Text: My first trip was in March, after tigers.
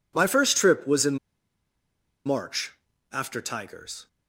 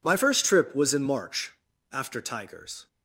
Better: second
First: pauses between "in" and "March"; at 1.1 s; 1.0 s long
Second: none

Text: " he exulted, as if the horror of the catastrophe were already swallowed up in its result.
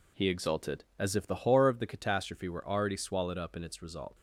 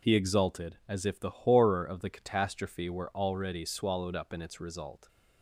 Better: neither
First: none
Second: none

